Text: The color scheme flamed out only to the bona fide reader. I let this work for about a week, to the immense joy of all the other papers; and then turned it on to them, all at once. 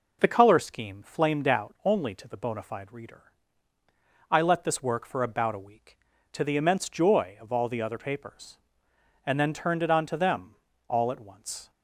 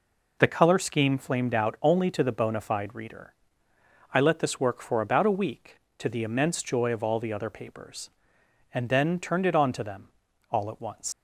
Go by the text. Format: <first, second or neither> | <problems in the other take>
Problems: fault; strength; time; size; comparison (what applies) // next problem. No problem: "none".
first | leaves "once" unfinished; at 11.1 s; 105 ms